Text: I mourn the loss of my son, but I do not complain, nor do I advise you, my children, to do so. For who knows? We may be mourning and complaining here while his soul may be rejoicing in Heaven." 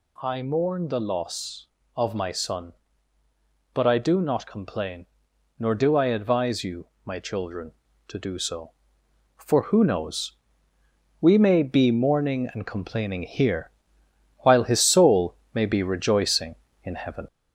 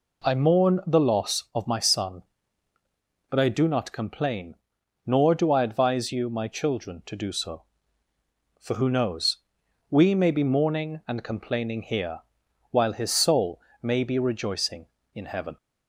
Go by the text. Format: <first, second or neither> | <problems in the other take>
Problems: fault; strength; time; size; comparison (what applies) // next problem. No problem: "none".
second | gets louder; slight; throughout; 2.5 dB // pauses between "here" and "while"; noticeable; at 13.6 s; 0.70 s long; noticeable in the second // pauses between "soul" and "may"; slight; at 15.3 s; 0.18 s long; slight in the second